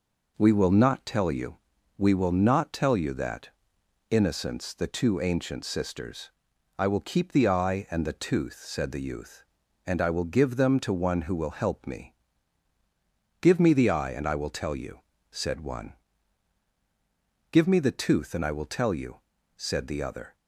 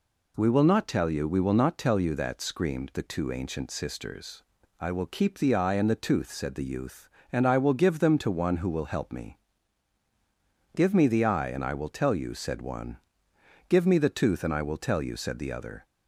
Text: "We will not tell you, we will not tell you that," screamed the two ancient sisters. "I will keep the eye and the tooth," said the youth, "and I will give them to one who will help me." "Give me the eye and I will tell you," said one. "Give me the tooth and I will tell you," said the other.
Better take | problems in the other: second | says "innocence" for "screamed"; at 4.1 s

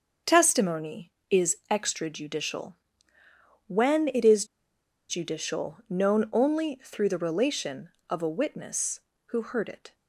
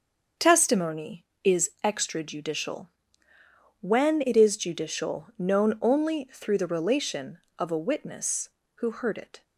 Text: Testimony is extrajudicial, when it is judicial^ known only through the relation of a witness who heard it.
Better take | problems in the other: second | starts louder than the rest; until 1.4 s; 6.5 dB; also in the second // pauses between "is" and "judicial"; noticeable; at 4.4 s; 0.63 s long

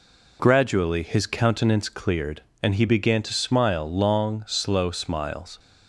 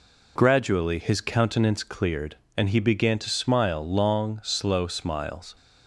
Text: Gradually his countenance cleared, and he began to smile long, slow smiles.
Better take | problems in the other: neither | none

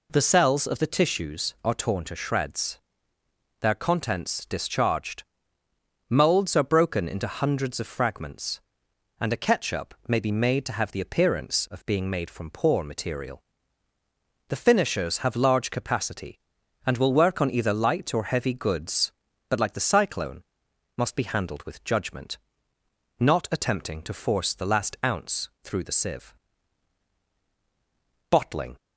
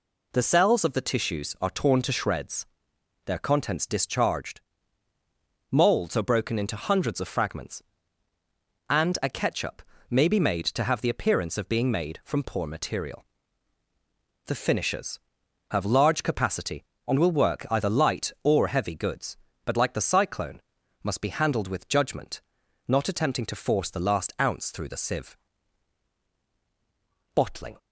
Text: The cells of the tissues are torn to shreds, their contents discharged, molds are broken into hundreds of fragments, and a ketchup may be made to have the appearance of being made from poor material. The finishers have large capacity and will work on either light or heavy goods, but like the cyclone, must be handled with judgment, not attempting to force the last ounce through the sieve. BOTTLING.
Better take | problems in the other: first | pauses between "ketchup" and "may"; slight; at 9.8 s; 0.30 s long // skips "on"; at 17.6 s

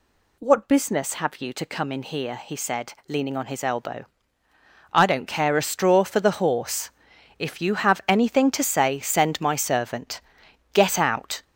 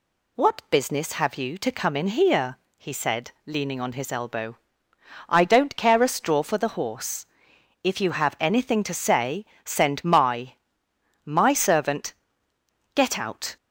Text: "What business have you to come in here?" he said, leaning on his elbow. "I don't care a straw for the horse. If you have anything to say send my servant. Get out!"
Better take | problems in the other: first | pauses between "say" and "send"; slight; at 9.4 s; 0.18 s long // says "my" twice; at 11.2 s

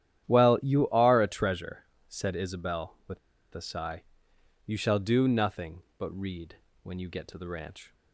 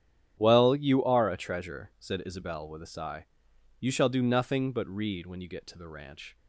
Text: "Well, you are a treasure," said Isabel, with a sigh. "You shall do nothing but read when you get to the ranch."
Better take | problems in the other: second | starts louder than the rest; strong; until 1.2 s; 11 dB; strong in the second // pauses between "with" and "a"; slight; at 3.1 s; 0.34 s long // pauses between "read" and "when"; slight; at 6.5 s; 0.26 s long

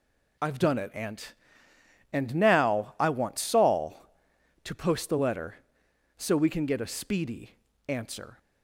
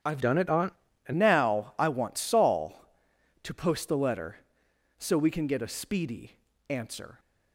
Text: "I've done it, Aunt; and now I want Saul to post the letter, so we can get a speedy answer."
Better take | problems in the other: first | starts louder than the rest; strong; until 1.3 s; 8.5 dB // changes voice from "done" to "and"; from 0.2 to 1.1 s; 0.9 s long // pauses between "speedy" and "answer"; slight; at 6.3 s; 0.32 s long; slight in the first

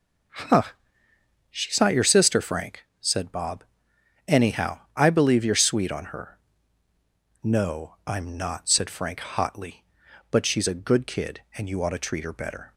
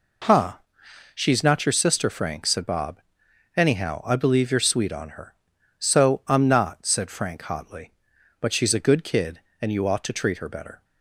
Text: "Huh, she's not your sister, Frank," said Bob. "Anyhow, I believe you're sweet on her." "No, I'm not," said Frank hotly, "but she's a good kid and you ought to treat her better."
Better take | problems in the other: first | says "So" for "No"; at 5.7 s

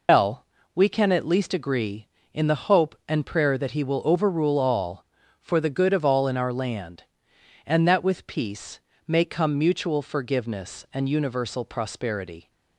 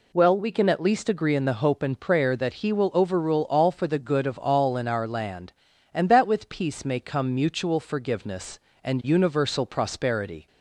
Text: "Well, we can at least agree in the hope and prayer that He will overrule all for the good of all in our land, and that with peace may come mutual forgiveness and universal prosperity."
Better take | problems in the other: second | loses the start of "Well"; at 0.0 s; 140 ms // pauses between "peace" and "may"; slight; at 8.8 s; 0.26 s long

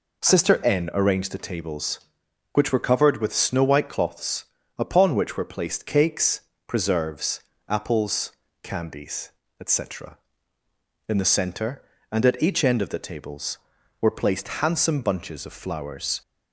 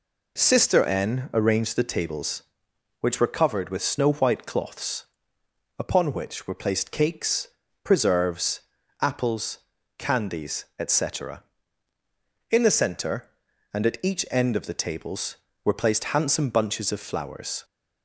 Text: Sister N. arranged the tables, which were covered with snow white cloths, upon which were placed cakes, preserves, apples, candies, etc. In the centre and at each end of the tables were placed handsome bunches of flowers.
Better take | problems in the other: neither | none

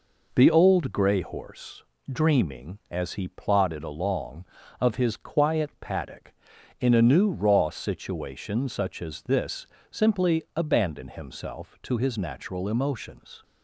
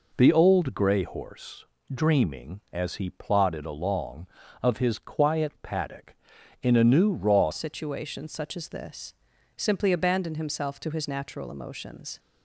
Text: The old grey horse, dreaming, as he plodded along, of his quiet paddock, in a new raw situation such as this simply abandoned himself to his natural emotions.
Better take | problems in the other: first | changes voice at "situation"; from 7.5 s on; 4.6 s long // pauses between "this" and "simply"; at 9.1 s; 0.42 s long; slight in the first

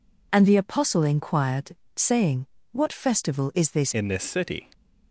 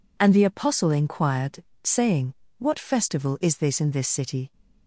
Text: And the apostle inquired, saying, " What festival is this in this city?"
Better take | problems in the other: second | changes voice at "in"; from 3.9 s on; 0.7 s long

